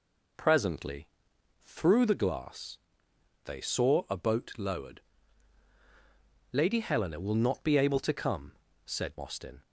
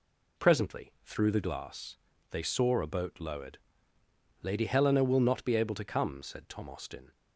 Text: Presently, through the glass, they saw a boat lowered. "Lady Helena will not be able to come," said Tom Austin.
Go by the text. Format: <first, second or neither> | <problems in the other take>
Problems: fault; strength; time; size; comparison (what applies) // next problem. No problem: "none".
second | skips "Tom"; at 9.1 s